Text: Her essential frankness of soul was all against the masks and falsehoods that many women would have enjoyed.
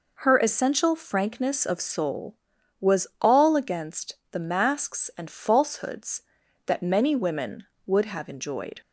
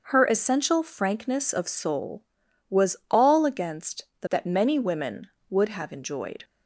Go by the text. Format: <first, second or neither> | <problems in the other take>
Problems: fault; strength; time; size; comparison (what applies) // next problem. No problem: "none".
first | starts louder than the rest; noticeable; until 1.0 s; 6 dB // pauses between "against" and "the"; slight; at 4.0 s; 0.16 s long; slight in the first // skips "masks and falsehoods"; at 4.2 s